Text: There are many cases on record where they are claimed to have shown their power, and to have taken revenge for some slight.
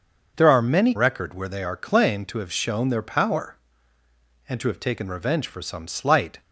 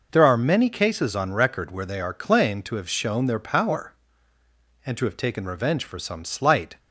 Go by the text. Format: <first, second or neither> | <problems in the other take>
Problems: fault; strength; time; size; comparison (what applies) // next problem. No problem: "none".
second | starts louder than the rest; until 1.3 s; 6 dB // skips "cases on"; at 0.9 s